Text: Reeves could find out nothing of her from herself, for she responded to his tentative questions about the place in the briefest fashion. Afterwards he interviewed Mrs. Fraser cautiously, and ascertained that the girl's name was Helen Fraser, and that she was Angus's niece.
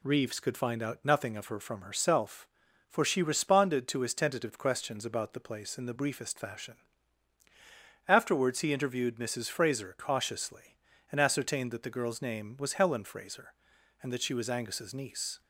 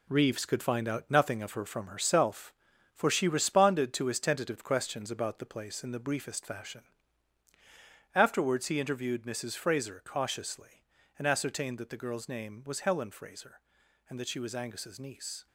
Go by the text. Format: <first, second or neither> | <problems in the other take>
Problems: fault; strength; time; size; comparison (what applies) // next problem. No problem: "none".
first | gets quieter; strong; throughout; 7.5 dB